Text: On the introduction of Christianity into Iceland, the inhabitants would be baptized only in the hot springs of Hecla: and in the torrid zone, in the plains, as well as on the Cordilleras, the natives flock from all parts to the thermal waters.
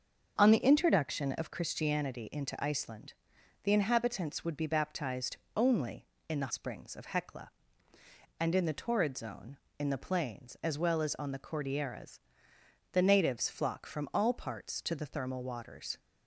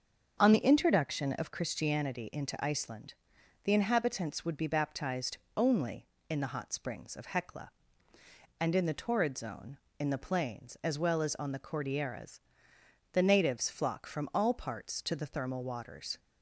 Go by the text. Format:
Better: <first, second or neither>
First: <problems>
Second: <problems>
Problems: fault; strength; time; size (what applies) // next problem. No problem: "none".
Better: second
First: starts louder than the rest; until 1.3 s; 6.5 dB // pauses between "baptized" and "only"; slight; at 5.3 s; 0.18 s long // skips "hot"; at 6.5 s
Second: starts louder than the rest; until 1.4 s; 6.5 dB // pauses between "baptized" and "only"; slight; at 5.3 s; 0.18 s long